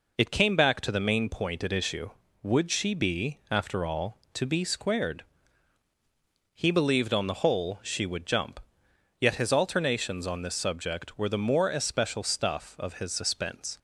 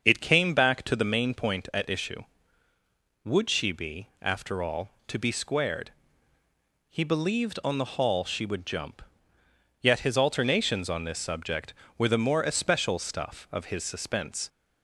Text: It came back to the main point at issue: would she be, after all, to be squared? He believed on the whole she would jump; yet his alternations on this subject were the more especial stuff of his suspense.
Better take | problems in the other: first | starts louder than the rest; until 1.0 s; 6.5 dB // says "hall" for "whole"; at 7.9 s

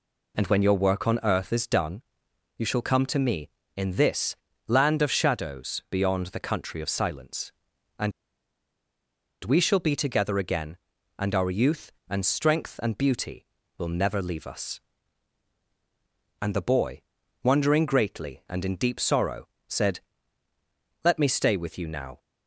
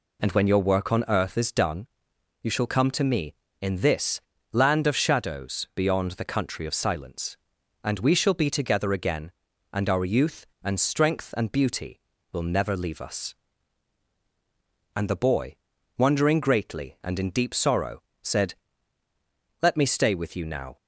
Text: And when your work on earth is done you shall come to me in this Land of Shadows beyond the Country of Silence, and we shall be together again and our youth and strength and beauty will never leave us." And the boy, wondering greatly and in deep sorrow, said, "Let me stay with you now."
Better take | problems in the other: second | pauses between "done" and "you"; noticeable; at 2.0 s; 0.56 s long; noticeable in the second // pauses between "this" and "Land"; slight; at 4.3 s; 0.32 s long; slight in the second // pauses between "and" and "we"; strong; at 8.1 s; 1.3 s long

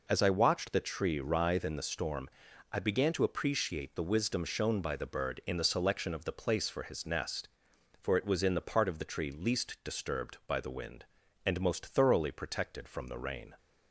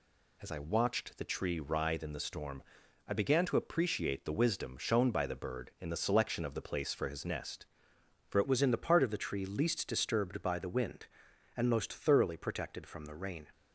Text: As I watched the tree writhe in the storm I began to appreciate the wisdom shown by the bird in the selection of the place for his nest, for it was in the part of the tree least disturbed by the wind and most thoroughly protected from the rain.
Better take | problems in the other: first | pauses between "storm" and "I"; noticeable; at 2.6 s; 0.46 s long; also in the first // changes voice at "was"; from 8.4 s on; 5.0 s long

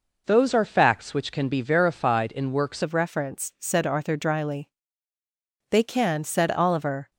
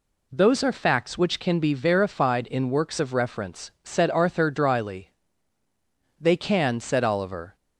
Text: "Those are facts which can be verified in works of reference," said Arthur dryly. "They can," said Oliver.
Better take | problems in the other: second | changes voice at "of"; from 2.8 s on; 4.3 s long

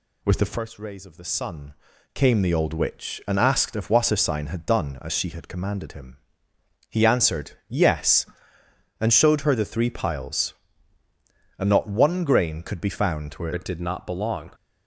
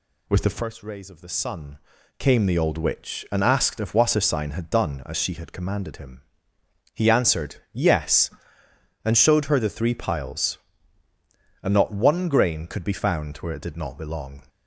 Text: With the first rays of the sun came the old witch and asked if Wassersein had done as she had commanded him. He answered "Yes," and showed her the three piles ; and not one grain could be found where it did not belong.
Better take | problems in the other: second | pauses between "sun" and "came"; at 1.7 s; 0.38 s long; also in the second // pauses between "answered" and "Yes"; slight; at 7.5 s; 0.16 s long; slight in the second // changes voice at "it"; from 13.5 s on; 1.0 s long

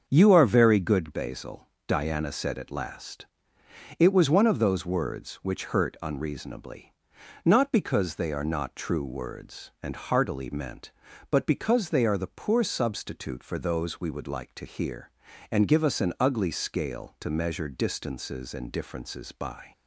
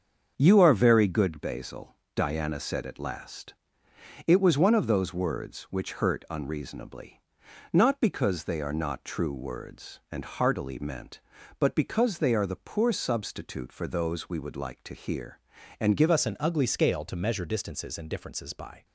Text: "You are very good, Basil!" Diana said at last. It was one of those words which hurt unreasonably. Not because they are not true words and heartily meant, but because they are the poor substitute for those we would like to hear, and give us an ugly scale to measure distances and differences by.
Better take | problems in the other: first | starts louder than the rest; until 1.3 s; 6.5 dB; also in the first // changes voice at "us"; from 16.1 s on; 2.7 s long

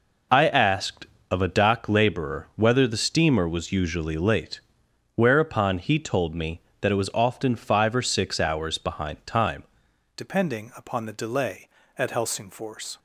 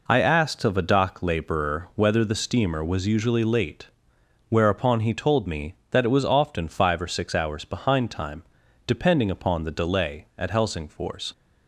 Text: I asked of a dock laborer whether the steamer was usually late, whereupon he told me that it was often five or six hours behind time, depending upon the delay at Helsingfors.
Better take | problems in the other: second | changes voice at "depending"; from 10.1 s on; 2.8 s long

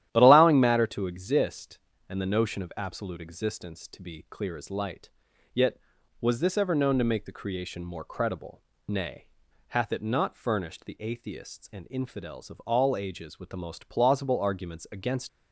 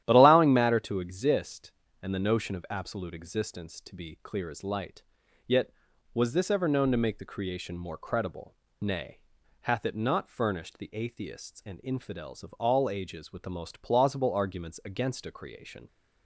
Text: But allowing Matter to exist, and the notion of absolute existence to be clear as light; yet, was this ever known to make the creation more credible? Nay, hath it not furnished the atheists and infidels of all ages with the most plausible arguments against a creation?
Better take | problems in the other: second | starts louder than the rest; strong; until 1.1 s; 12 dB; strong in the second // stops before "a creation"; at 15.2 s

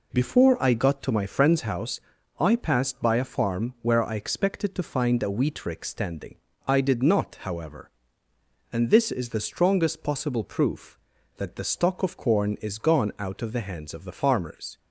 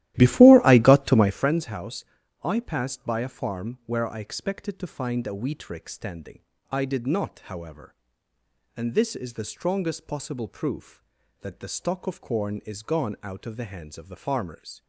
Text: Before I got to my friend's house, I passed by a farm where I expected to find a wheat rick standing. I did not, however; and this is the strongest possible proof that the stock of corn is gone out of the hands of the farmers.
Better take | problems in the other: first | starts louder than the rest; strong; until 1.5 s; 14.5 dB

